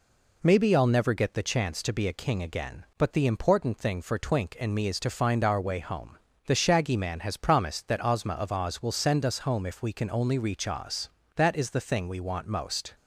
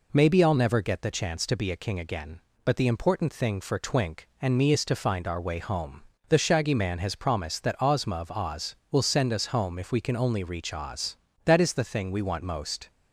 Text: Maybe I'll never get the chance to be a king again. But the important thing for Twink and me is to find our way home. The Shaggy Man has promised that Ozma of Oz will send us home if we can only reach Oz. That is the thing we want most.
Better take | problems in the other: neither | none

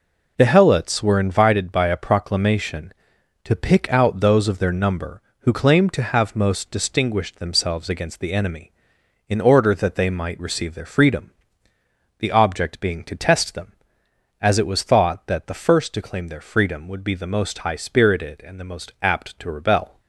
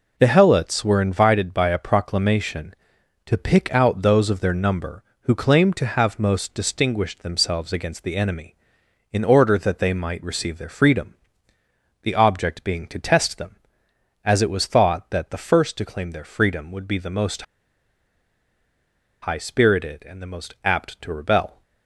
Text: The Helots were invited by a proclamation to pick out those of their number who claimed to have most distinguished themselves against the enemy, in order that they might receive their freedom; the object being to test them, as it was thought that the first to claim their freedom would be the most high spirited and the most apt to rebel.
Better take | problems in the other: first | pauses between "most" and "high"; strong; at 17.4 s; 1.7 s long

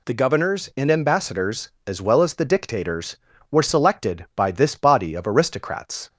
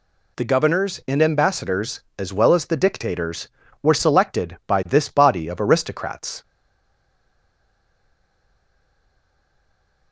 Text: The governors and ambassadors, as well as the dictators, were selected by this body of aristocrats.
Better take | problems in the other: first | stays silent after the last word; strong; from 6.4 s on; 3.7 s long

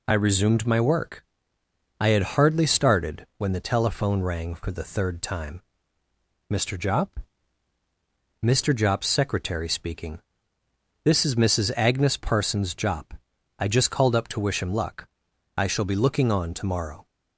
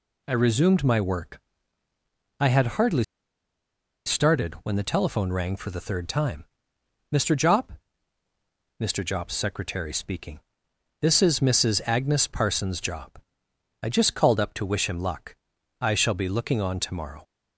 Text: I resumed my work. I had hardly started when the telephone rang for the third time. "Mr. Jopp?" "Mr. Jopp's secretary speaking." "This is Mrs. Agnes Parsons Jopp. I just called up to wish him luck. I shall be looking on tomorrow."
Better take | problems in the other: first | pauses between "hardly" and "started"; at 3.0 s; 1.0 s long

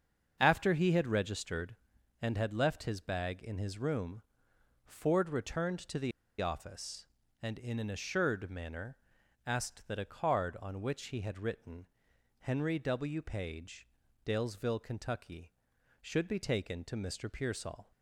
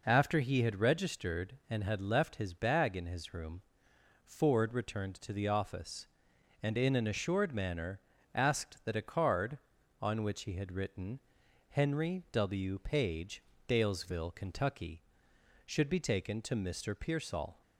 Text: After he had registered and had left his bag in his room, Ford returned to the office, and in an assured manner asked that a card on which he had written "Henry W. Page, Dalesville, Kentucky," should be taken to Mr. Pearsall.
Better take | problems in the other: second | starts louder than the rest; until 1.4 s; 7 dB // pauses between "the" and "office"; slight; at 6.1 s; 0.29 s long // pauses between "manner" and "asked"; noticeable; at 8.9 s; 0.48 s long; slight in the second // pauses between "written" and "Henry"; noticeable; at 11.8 s; 0.54 s long; noticeable in the second

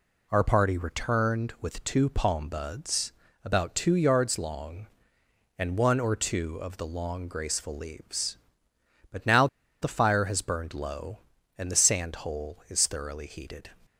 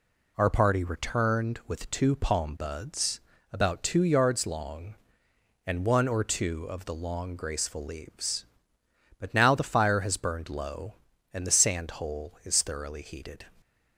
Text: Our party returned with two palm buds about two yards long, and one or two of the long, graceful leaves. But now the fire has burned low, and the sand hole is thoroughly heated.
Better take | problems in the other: second | pauses between "buds" and "about"; slight; at 3.1 s; 0.32 s long; slight in the second // pauses between "now" and "the"; slight; at 9.4 s; 0.35 s long

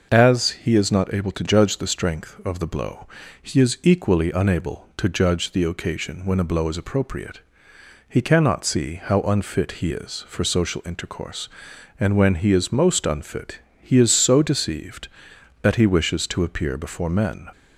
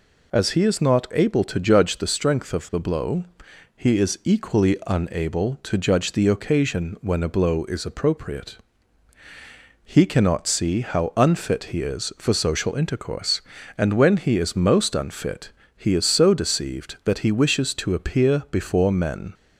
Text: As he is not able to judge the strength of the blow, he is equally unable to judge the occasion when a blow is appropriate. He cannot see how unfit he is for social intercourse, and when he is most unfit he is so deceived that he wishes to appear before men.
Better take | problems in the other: neither | pauses between "unfit" and "he"; slight; the same in both

